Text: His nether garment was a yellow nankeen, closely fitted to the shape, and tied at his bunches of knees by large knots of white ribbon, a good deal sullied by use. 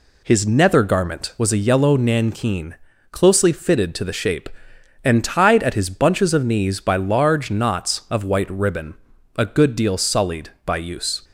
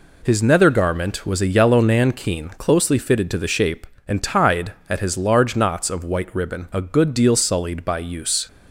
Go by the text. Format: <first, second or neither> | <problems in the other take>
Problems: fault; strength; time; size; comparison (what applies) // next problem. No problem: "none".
first | skips "bunches of knees by"; at 5.1 s